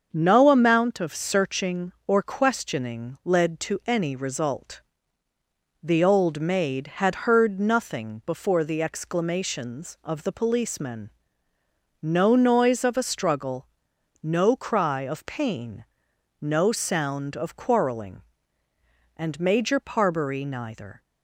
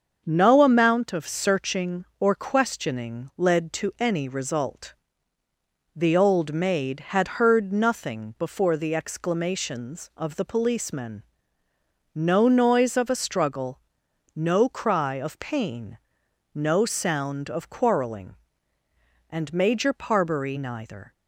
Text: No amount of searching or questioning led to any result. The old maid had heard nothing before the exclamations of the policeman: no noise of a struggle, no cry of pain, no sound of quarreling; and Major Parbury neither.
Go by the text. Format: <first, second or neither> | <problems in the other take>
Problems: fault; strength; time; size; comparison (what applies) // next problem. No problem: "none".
neither | starts louder than the rest; the same in both